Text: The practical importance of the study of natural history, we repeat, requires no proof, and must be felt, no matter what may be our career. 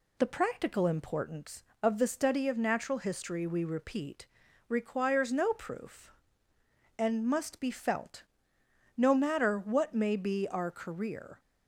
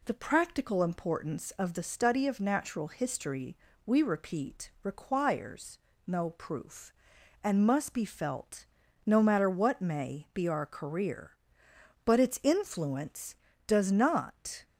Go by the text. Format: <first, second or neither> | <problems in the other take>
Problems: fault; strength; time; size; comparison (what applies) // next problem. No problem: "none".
first | pauses between "requires" and "no"; slight; at 5.7 s; 0.28 s long // goes on to say "But its influence does not"; strong; from 12.0 s on; 2.6 s long